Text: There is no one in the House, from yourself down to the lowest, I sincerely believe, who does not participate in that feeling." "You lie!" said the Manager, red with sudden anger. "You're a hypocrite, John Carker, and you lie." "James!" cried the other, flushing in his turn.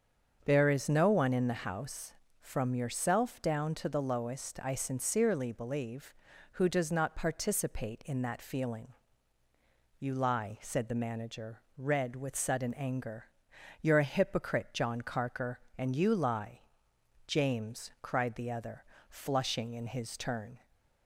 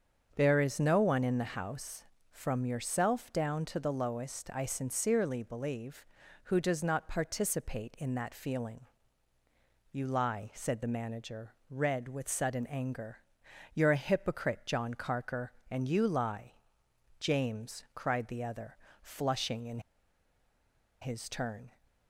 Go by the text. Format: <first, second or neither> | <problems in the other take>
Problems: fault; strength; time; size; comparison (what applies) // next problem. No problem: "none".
first | starts louder than the rest; strong; until 1.3 s; 7.5 dB; also in the first // pauses between "in" and "his"; at 19.7 s; 1.2 s long